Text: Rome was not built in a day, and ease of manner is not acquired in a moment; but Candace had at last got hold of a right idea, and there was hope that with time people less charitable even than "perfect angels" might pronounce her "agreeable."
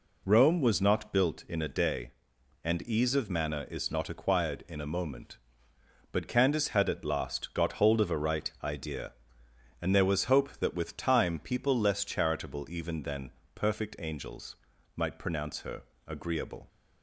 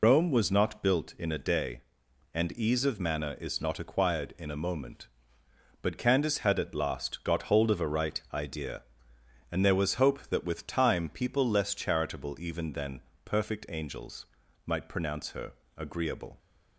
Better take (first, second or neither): first